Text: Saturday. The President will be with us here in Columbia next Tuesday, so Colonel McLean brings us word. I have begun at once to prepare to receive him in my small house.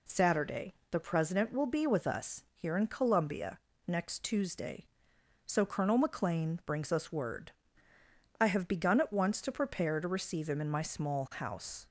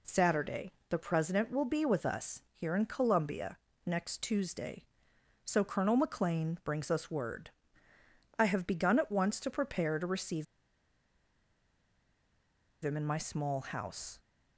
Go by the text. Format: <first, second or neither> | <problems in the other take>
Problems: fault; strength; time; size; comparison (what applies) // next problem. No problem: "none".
first | pauses between "Columbia" and "next"; slight; at 3.5 s; 0.28 s long; slight in the first // pauses between "receive" and "him"; strong; at 10.4 s; 2.3 s long